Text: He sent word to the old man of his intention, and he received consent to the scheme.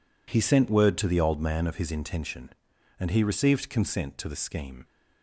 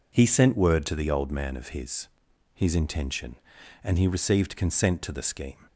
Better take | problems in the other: first | says "his" twice; at 2.5 s

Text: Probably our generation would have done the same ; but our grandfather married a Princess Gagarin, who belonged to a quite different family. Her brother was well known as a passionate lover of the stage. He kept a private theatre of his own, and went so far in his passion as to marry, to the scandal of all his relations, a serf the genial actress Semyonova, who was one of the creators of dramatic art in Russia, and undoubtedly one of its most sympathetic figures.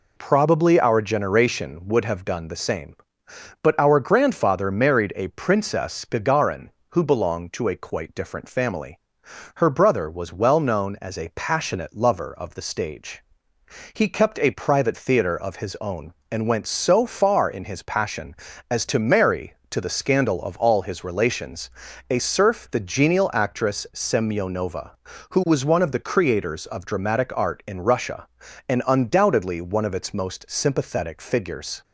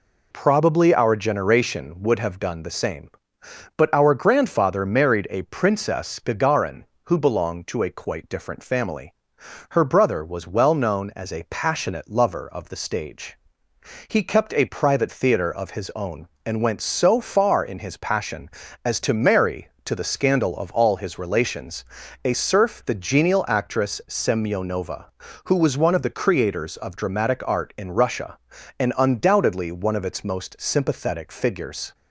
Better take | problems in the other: neither | none

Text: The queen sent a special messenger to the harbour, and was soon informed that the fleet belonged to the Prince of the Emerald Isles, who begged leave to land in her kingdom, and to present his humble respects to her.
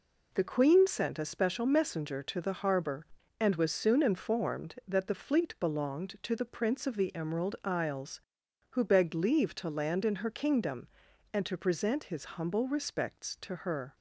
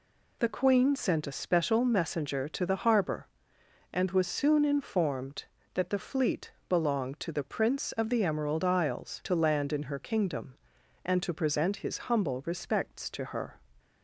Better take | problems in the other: first | pauses between "fleet" and "belonged"; slight; at 6.5 s; 0.18 s long // skips "who begged leave"; at 9.2 s

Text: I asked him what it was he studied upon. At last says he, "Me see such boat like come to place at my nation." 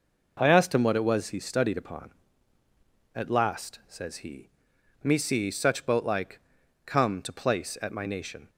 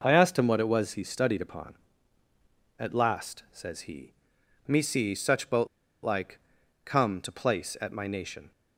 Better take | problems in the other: first | pauses between "boat" and "like"; slight; at 5.6 s; 0.35 s long // pauses between "like" and "come"; noticeable; at 6.3 s; 0.48 s long; noticeable in the first

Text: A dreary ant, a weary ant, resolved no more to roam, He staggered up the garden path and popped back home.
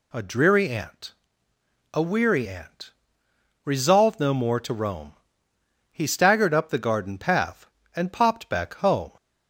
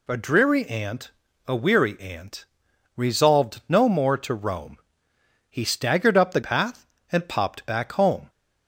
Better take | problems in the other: first | skips "garden"; at 6.4 s

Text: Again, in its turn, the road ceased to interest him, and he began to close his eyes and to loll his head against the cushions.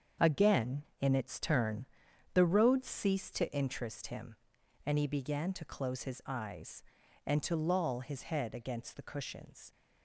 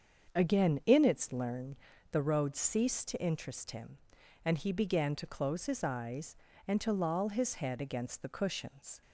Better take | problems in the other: first | starts louder than the rest; until 1.4 s; 7 dB; strong in the first // says "learn" for "turn"; at 1.3 s

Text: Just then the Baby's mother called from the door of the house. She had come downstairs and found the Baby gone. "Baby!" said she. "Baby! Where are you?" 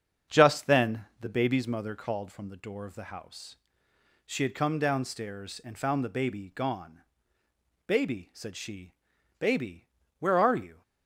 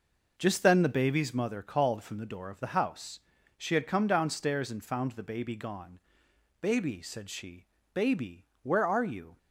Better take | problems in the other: second | starts louder than the rest; strong; until 1.7 s; 7.5 dB

